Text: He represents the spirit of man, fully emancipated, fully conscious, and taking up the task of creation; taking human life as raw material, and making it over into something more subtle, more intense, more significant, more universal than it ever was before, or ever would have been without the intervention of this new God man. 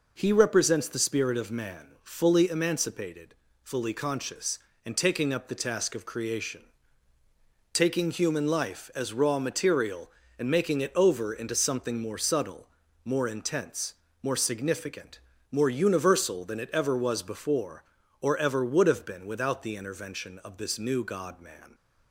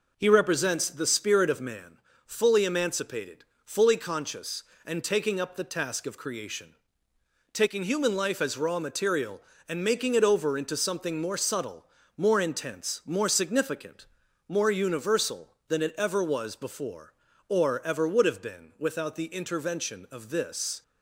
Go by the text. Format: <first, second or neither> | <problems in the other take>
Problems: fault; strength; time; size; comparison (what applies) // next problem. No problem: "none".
first | stops before "new God man"; at 20.8 s